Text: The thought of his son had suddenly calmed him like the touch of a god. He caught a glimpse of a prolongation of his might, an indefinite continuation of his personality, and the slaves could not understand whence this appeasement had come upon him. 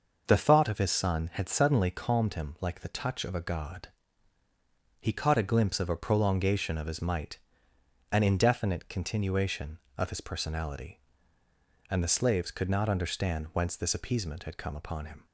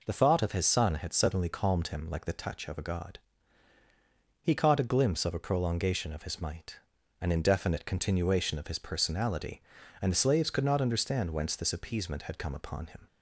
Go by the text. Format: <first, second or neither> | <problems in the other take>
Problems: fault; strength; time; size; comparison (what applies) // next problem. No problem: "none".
neither | none